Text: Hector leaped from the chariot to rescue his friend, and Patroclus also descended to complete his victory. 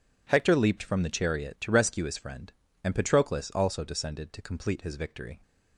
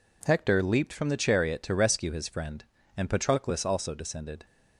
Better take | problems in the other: first | stops before "to complete his victory"; at 4.4 s

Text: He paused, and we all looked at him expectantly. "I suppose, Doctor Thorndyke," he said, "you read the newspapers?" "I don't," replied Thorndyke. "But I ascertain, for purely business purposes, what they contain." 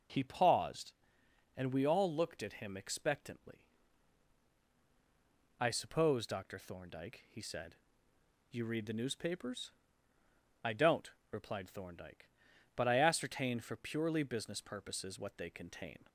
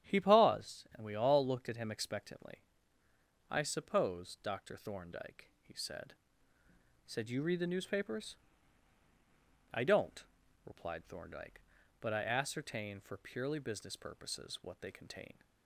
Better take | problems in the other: first | starts louder than the rest; strong; until 1.1 s; 10 dB // says "said" twice; at 7.0 s

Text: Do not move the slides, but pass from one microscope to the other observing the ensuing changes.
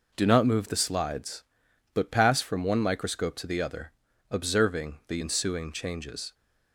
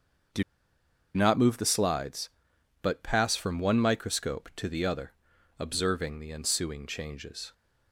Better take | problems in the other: first | starts louder than the rest; until 2.0 s; 6.5 dB // pauses between "Do" and "not"; noticeable; at 0.4 s; 0.71 s long // pauses between "other" and "observing"; noticeable; at 5.1 s; 0.46 s long; also in the first

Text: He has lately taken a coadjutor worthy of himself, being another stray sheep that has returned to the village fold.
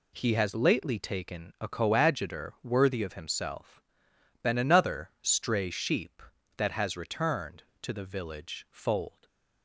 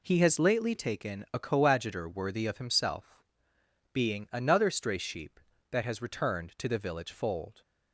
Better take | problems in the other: second | says "been" for "being"; at 4.4 s // stays silent after the last word; slight; from 9.0 s on; 0.6 s long

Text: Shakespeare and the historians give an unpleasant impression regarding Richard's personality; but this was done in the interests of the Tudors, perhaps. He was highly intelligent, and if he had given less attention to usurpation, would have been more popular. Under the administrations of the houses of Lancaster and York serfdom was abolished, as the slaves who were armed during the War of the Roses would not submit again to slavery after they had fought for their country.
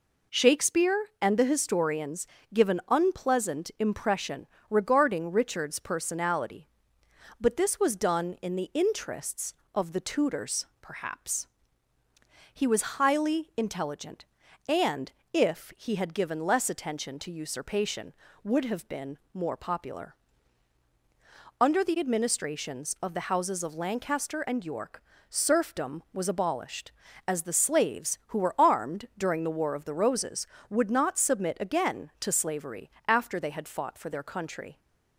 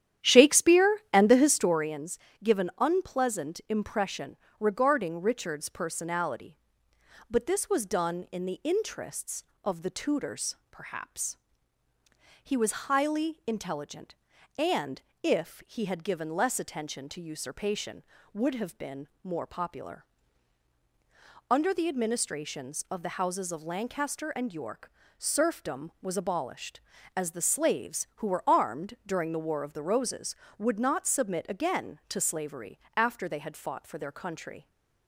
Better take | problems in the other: first | starts louder than the rest; strong; until 1.9 s; 11 dB // pauses between "historians" and "give"; slight; at 2.1 s; 0.24 s long; slight in the first // pauses between "impression" and "regarding"; slight; at 4.3 s; 0.24 s long; slight in the first // pauses between "and" and "if"; slight; at 15.0 s; 0.22 s long; slight in the first // pauses between "been" and "more"; slight; at 19.0 s; 0.16 s long; slight in the first // pauses between "York" and "serfdom"; slight; at 24.9 s; 0.30 s long; slight in the first // pauses between "slavery" and "after"; slight; at 32.7 s; 0.16 s long; slight in the first

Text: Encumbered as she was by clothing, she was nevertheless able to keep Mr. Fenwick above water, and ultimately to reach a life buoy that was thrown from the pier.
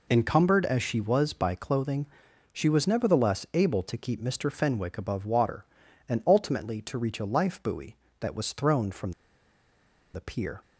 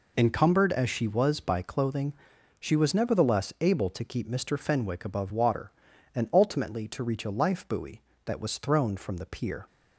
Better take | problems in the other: second | pauses between "from" and "the"; at 9.1 s; 1.0 s long

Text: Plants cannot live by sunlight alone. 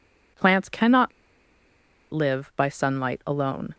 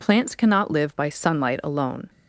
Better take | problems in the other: second | pauses between "cannot" and "live"; at 1.1 s; 1.0 s long

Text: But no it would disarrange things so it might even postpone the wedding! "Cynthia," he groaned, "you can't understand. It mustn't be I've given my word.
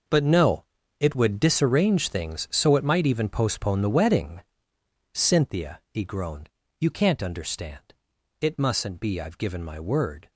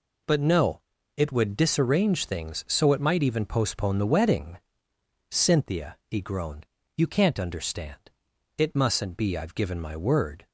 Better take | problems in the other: second | gets quieter; strong; throughout; 13 dB // pauses between "no" and "it"; slight; at 0.6 s; 0.36 s long; slight in the second

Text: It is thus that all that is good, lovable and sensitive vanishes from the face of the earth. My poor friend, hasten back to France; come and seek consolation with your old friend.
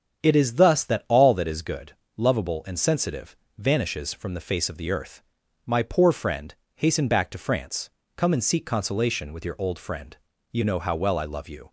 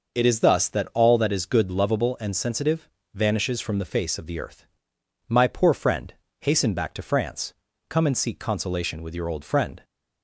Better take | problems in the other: second | starts louder than the rest; strong; until 1.2 s; 8 dB // pauses between "sensitive" and "vanishes"; slight; at 3.3 s; 0.20 s long; slight in the second // goes on to say "You know how well I love you"; noticeable; from 10.5 s on; 1.2 s long

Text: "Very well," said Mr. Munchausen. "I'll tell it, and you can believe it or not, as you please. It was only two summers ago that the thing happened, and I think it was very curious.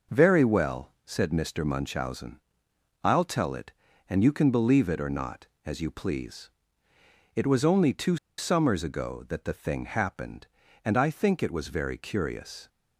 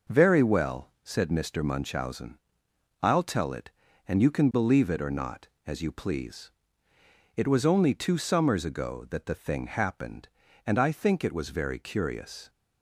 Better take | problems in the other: second | pauses between "two" and "summers"; slight; at 8.1 s; 0.21 s long

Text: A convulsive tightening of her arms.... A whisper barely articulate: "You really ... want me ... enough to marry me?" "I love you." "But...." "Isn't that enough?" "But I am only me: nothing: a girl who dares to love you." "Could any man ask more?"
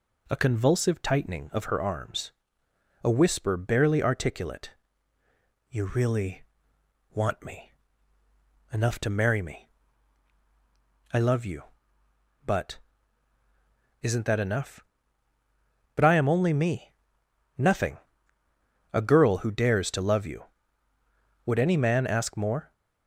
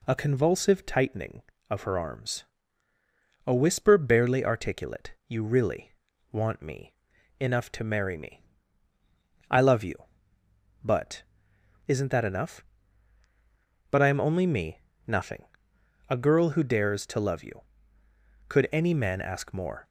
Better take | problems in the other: second | says "Would" for "Could"; at 21.4 s

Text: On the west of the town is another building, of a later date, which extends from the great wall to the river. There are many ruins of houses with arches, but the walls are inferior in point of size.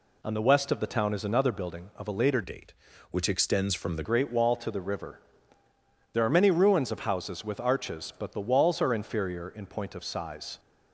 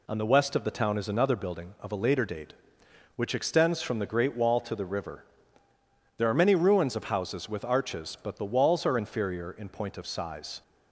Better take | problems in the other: second | changes voice from "date" to "the"; from 2.4 to 4.0 s; 1.6 s long

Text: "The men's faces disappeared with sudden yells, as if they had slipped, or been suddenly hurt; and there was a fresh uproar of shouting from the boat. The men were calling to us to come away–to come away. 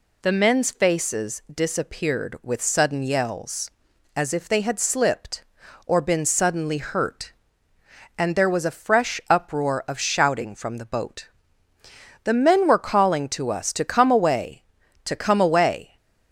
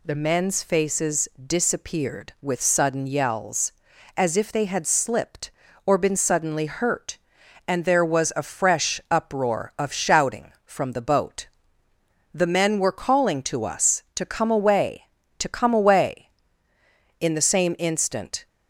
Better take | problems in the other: first | goes on to say "In the same instant"; noticeable; from 17.1 s on; 1.2 s long

